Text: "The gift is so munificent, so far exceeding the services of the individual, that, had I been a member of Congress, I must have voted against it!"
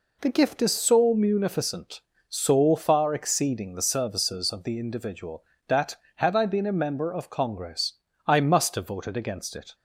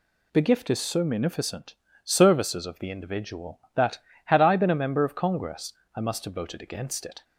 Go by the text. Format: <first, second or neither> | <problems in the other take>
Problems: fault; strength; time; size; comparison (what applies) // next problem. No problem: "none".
first | skips "so far exceeding the"; at 1.8 s